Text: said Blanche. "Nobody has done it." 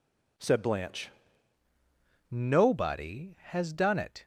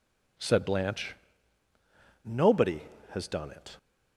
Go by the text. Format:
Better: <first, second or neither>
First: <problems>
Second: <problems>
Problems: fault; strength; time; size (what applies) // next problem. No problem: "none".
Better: second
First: changes voice at "Nobody"; from 2.3 s on; 1.9 s long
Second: none